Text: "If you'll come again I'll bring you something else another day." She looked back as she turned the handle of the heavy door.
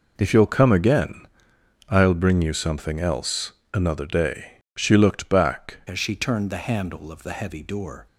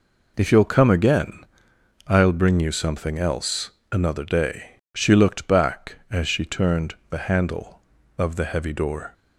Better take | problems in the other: second | pauses between "again" and "I'll"; noticeable; at 1.2 s; 0.62 s long; noticeable in the second // pauses between "else" and "another"; slight; at 3.5 s; 0.22 s long; slight in the second // changes voice at "as"; from 5.8 s on; 2.2 s long

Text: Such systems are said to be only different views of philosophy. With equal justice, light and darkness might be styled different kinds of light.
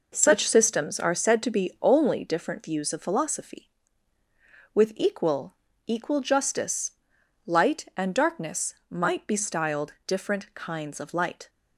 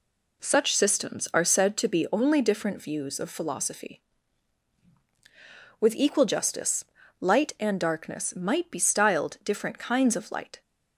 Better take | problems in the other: second | says "equal" twice; at 5.8 s // pauses between "darkness" and "might"; slight; at 8.7 s; 0.16 s long

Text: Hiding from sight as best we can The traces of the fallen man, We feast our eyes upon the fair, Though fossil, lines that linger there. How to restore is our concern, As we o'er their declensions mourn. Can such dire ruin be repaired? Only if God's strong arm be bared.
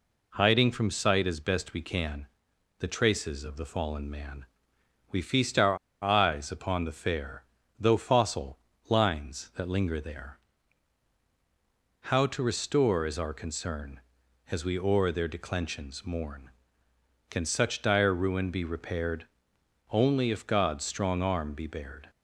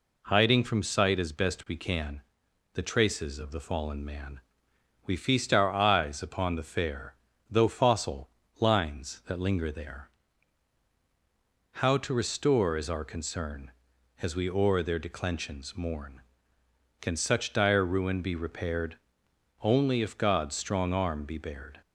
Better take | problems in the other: second | pauses between "can" and "The"; noticeable; at 2.2 s; 0.52 s long; noticeable in the second // pauses between "our" and "eyes"; slight; at 5.7 s; 0.26 s long

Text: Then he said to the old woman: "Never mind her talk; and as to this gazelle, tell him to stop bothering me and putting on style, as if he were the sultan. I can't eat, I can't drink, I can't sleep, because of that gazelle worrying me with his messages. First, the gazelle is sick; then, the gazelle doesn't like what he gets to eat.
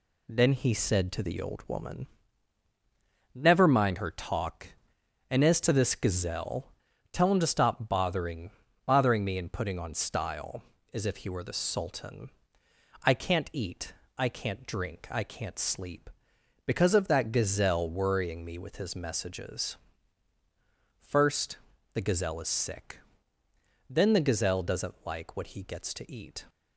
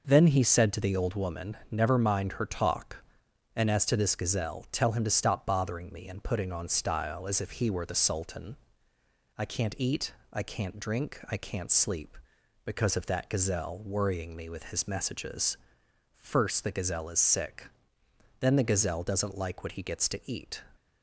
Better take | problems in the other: second | says "bothering" twice; at 8.8 s

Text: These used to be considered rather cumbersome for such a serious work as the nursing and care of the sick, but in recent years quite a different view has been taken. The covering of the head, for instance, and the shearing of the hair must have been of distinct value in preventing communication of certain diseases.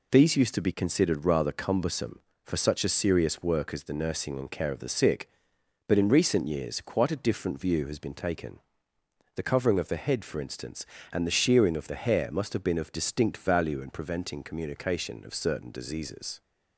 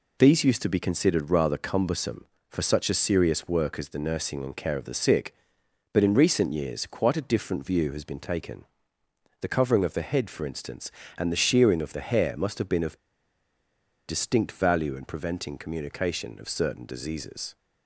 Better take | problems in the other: first | pauses between "of" and "distinct"; at 12.9 s; 1.0 s long

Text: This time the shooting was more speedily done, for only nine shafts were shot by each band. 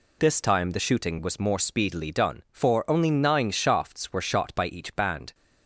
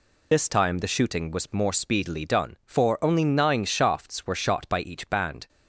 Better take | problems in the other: first | loses the start of "This"; at 0.3 s; 35 ms

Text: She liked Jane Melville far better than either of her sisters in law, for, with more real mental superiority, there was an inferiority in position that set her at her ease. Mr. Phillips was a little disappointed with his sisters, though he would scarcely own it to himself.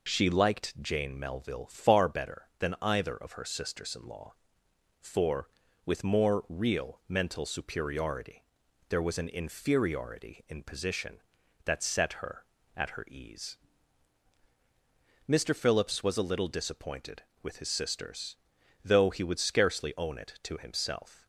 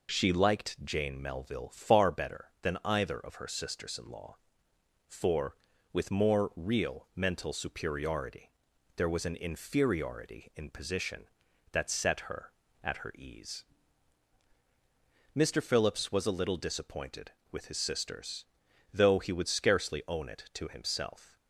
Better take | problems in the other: neither | none

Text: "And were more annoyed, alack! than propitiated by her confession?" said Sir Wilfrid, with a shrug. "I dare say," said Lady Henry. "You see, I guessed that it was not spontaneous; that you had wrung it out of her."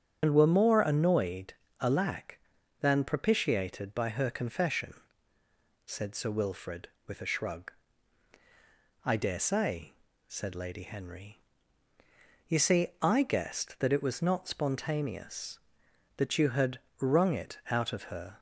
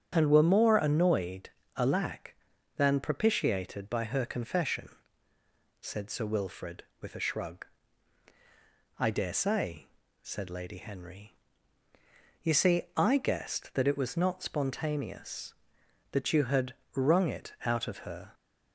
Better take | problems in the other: second | loses the start of "And"; at 0.2 s; 65 ms // starts louder than the rest; strong; until 1.2 s; 8 dB; strong in the second // pauses between "had" and "wrung"; slight; at 16.7 s; 0.20 s long; slight in the second

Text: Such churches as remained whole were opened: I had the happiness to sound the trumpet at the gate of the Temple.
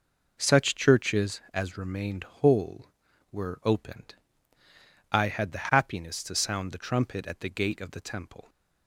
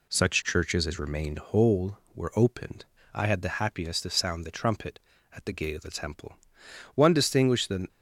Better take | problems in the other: first | goes on to say "One distinguished the"; noticeable; from 6.9 s on; 0.94 s long

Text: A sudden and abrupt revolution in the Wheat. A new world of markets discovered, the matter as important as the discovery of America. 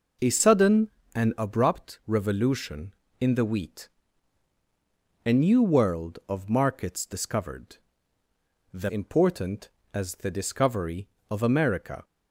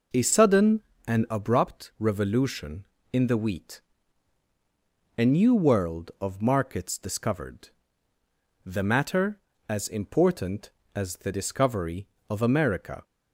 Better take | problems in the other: second | skips "matter as"; at 8.8 s

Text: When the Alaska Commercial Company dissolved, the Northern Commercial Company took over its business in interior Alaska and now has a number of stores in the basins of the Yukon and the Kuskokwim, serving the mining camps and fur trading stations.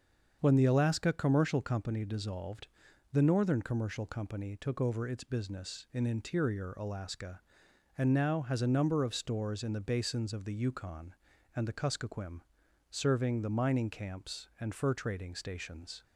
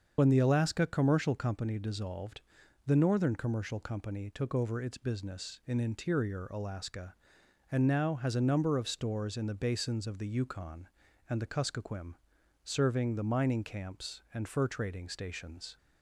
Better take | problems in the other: first | loses the start of "When"; at 0.1 s; 35 ms // starts louder than the rest; until 1.1 s; 7 dB; also in the first

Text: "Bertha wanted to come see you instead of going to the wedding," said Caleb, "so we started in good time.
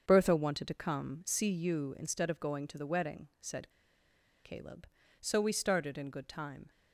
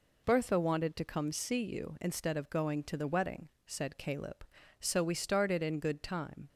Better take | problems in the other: second | starts louder than the rest; until 1.0 s; 6.5 dB // pauses between "said" and "Caleb"; noticeable; at 3.6 s; 0.75 s long

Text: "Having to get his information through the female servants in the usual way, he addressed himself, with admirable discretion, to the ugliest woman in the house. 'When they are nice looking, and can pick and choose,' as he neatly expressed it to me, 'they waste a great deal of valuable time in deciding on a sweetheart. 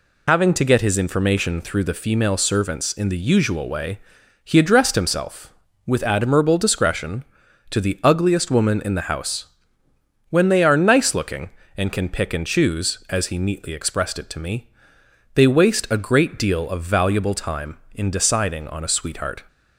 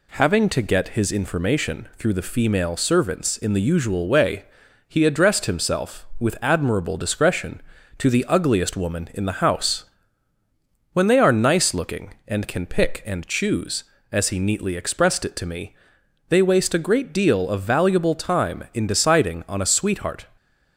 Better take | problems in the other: second | loses the start of "Having"; at 0.2 s; 85 ms

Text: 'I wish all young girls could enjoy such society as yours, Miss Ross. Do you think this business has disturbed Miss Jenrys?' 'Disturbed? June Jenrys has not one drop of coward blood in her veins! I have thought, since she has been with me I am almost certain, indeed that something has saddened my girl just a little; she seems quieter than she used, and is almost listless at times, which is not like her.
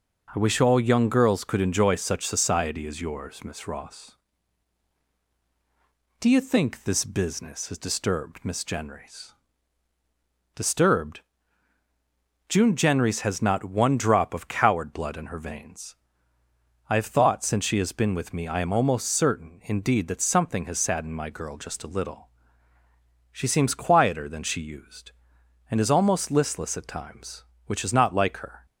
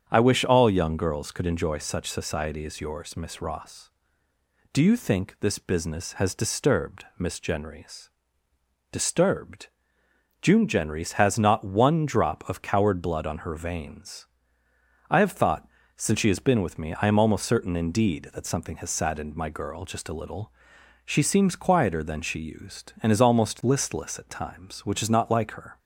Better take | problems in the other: first | starts louder than the rest; strong; until 1.0 s; 7.5 dB // says "on" for "in"; at 13.2 s

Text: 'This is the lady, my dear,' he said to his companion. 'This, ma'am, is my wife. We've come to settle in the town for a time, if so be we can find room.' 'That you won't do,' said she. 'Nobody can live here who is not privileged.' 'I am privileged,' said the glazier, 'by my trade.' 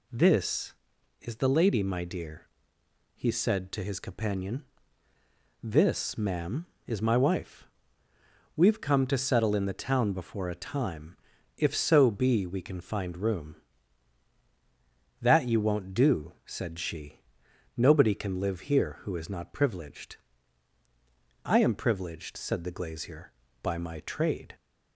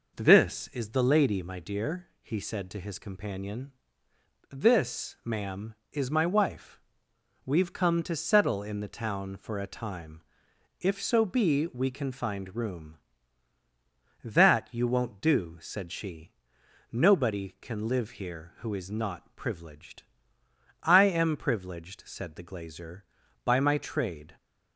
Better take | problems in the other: second | says "before" for "for"; at 10.1 s

